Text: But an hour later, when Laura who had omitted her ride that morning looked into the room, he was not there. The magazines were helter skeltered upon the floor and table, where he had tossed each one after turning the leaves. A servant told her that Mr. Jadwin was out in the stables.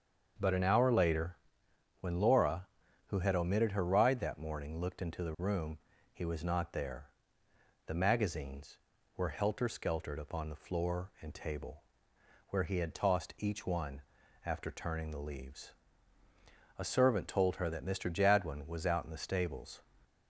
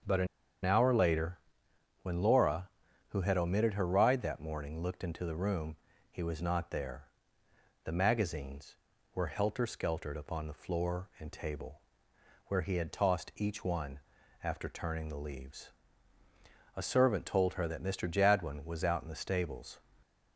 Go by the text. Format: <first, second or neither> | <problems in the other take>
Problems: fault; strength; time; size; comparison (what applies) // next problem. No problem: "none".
first | starts louder than the rest; until 2.1 s; 6.5 dB; also in the first // pauses between "an" and "hour"; at 0.2 s; 0.37 s long // pauses between "one" and "after"; at 13.9 s; 0.44 s long; also in the first